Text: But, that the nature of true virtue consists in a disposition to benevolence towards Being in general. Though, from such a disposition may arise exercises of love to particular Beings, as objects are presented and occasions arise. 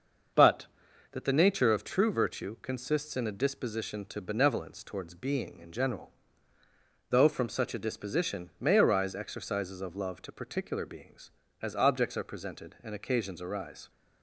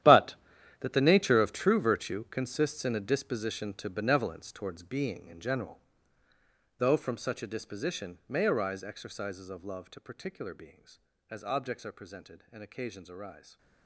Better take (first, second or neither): first